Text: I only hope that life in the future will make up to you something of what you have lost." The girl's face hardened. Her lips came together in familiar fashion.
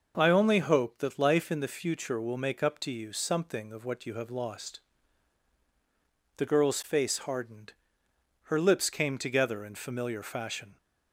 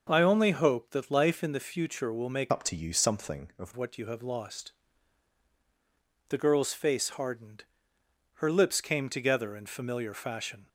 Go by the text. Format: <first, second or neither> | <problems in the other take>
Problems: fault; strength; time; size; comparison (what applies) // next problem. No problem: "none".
first | starts louder than the rest; noticeable; until 1.1 s; 6 dB // changes voice from "up" to "of"; from 2.5 to 3.7 s; 1.2 s long